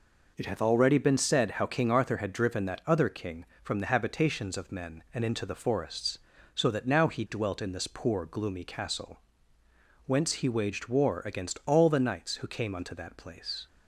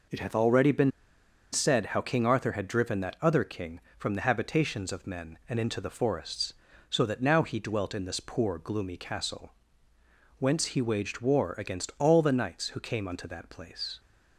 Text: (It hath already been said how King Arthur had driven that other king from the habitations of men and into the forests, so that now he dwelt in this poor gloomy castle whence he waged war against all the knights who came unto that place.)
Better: first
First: pauses between "castle" and "whence"; noticeable; at 9.2 s; 0.84 s long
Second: pauses between "been" and "said"; noticeable; at 0.8 s; 0.62 s long // pauses between "castle" and "whence"; noticeable; at 9.5 s; 0.84 s long

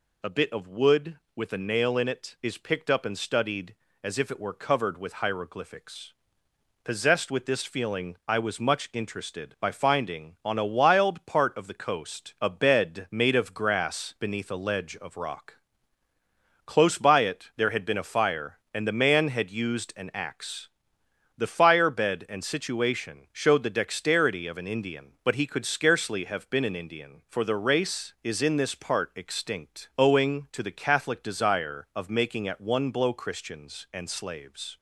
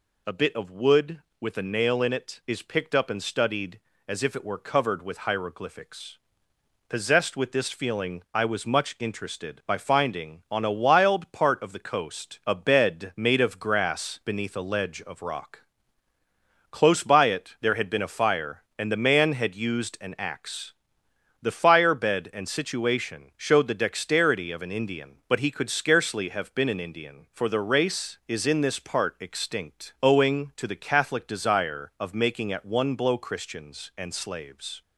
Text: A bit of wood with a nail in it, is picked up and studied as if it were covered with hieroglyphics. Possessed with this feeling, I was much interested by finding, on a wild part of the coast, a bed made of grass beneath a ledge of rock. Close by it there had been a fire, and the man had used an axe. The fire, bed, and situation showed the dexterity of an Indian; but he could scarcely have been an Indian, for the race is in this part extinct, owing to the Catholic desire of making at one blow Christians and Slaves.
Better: neither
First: none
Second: none

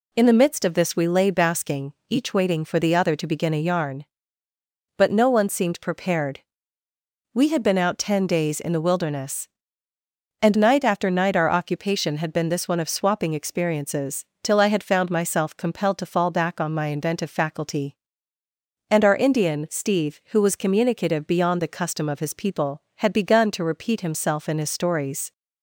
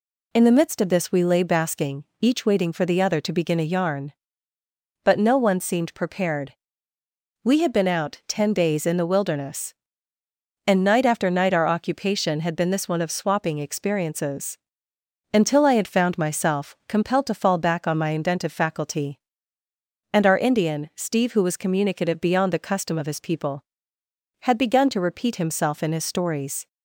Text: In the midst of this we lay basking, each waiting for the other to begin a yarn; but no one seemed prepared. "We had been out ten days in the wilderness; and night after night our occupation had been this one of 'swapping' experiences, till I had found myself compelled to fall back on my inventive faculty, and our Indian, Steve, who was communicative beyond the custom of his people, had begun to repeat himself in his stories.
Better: first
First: none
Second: says "until" for "till"; at 15.3 s

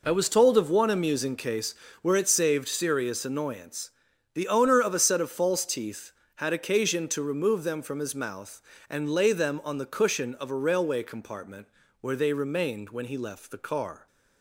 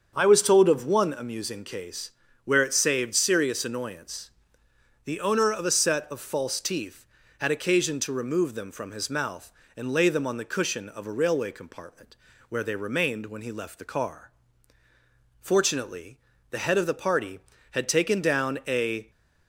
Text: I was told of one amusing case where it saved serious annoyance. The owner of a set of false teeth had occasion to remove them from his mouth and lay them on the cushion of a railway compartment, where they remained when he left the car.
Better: first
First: pauses between "case" and "where"; slight; at 1.7 s; 0.28 s long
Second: starts louder than the rest; until 1.1 s; 7 dB // pauses between "case" and "where"; slight; at 2.1 s; 0.32 s long // goes on to say "Fortunately the head of the party had taken down a"; strong; from 15.4 s on; 3.7 s long

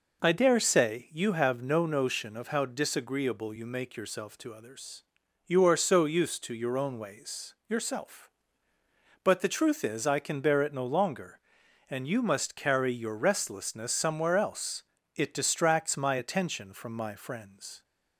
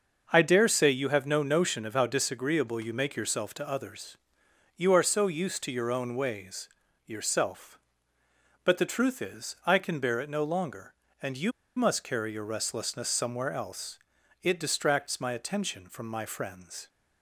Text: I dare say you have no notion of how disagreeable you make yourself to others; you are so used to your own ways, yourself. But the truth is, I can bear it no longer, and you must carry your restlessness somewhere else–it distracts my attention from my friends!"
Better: first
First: none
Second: starts louder than the rest; until 1.3 s; 6 dB // pauses between "you" and "must"; slight; at 11.5 s; 0.24 s long

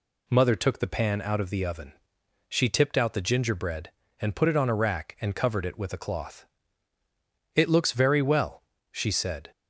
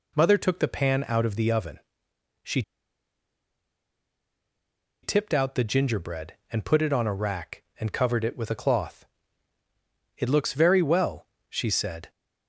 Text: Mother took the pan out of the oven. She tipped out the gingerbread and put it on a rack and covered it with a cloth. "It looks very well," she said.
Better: first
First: none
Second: pauses between "She" and "tipped"; strong; at 2.6 s; 2.4 s long

